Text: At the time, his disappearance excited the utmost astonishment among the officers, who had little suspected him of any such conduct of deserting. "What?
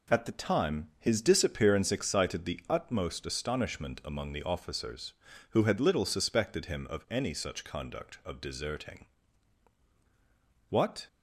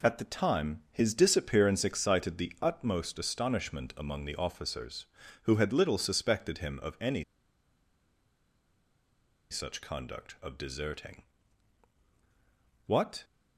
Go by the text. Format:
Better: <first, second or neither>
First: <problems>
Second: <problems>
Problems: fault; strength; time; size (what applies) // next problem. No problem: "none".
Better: first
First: none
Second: pauses between "any" and "such"; strong; at 7.2 s; 2.2 s long